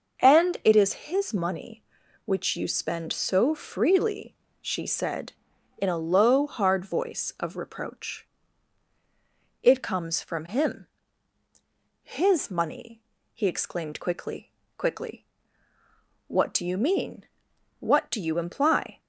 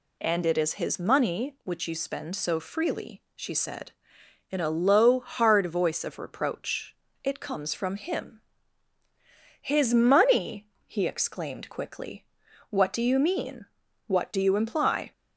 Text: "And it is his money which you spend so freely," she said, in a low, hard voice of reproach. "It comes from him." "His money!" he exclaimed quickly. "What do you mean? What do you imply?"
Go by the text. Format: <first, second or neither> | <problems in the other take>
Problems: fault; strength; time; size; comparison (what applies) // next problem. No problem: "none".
second | says "quickly" twice; at 14.7 s